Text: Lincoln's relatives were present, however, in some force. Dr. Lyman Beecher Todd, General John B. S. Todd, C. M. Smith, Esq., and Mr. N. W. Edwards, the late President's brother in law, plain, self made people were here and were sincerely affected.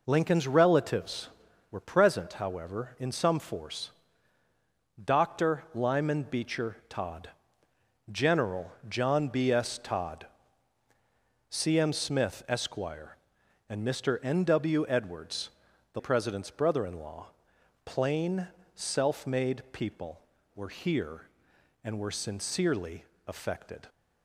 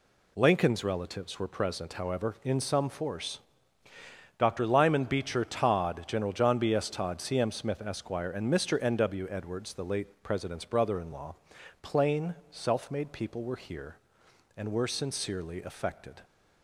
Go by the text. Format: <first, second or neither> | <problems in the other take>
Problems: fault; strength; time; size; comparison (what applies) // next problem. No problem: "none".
second | pauses between "General" and "John"; slight; at 8.6 s; 0.18 s long // skips "late"; at 16.0 s // pauses between "sincerely" and "affected"; slight; at 23.0 s; 0.24 s long